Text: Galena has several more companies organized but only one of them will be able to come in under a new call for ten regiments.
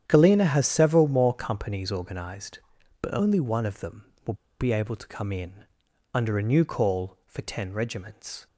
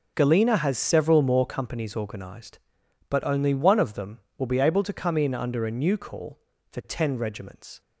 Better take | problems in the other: second | starts louder than the rest; strong; until 1.0 s; 9.5 dB // pauses between "will" and "be"; slight; at 4.3 s; 0.26 s long // pauses between "in" and "under"; noticeable; at 5.6 s; 0.48 s long

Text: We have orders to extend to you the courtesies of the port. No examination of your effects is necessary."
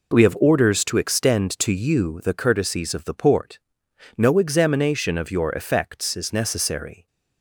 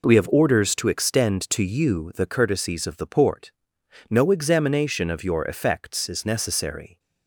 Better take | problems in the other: neither | none

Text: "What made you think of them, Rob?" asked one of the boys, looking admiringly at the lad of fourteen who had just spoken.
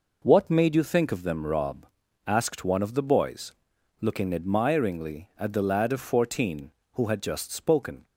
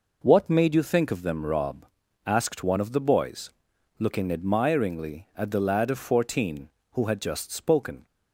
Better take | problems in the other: neither | none

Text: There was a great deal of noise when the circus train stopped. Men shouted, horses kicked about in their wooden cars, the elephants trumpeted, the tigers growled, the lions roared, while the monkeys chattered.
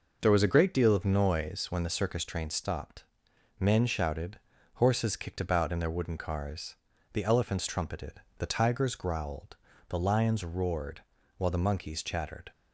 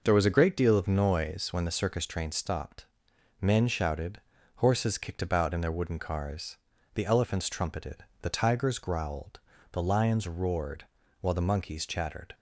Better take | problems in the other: neither | none

